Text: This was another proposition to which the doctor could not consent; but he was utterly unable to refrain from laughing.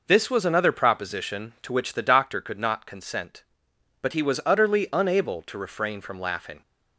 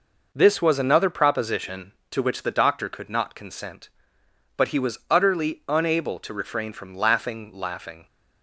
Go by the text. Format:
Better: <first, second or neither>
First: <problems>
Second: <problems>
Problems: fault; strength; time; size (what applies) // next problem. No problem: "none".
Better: first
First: none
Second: says "laughing" twice; at 7.5 s